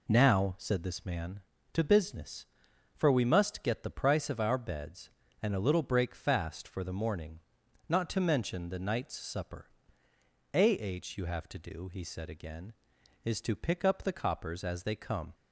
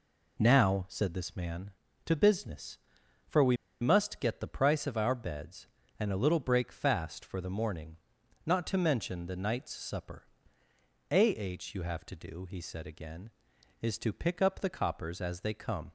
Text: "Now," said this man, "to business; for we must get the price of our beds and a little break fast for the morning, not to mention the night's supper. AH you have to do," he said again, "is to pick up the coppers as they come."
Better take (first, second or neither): first